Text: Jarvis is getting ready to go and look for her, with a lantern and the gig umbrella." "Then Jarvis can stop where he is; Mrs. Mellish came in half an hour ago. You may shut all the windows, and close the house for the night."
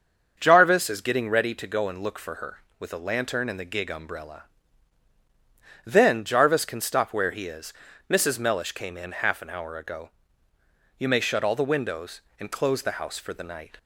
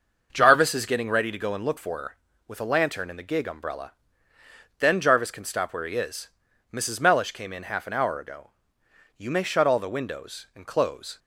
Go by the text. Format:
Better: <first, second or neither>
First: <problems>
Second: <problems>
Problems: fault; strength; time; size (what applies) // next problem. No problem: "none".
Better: first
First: starts louder than the rest; until 1.4 s; 6.5 dB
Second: starts louder than the rest; noticeable; until 1.3 s; 6 dB // stops before "the house for the night"; at 11.1 s